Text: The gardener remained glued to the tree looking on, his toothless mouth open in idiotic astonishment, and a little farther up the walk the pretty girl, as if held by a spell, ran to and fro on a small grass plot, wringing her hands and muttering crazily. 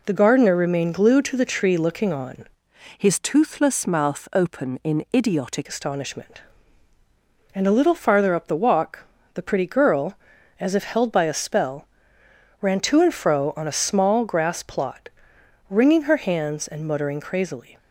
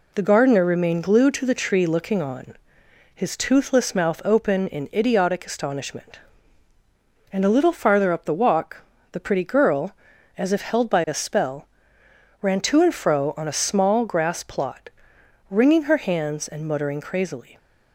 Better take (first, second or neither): second